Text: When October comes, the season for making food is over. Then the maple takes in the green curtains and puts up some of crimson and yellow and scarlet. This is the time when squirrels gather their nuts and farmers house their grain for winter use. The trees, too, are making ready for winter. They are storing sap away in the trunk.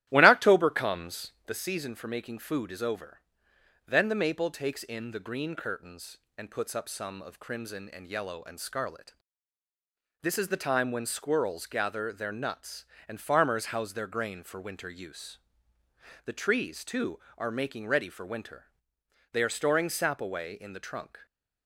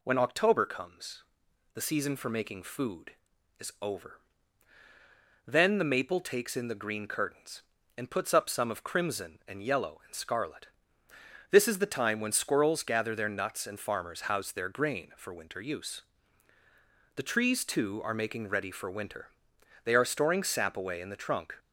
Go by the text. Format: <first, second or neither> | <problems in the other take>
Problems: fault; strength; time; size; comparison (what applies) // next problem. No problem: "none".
second | starts louder than the rest; strong; until 1.7 s; 13.5 dB